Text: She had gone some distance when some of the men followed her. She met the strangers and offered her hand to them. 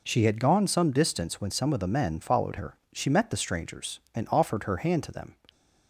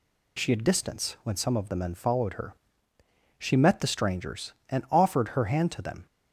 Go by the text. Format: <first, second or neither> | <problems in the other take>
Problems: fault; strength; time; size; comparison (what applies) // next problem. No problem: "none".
first | skips "gone some"; at 0.6 s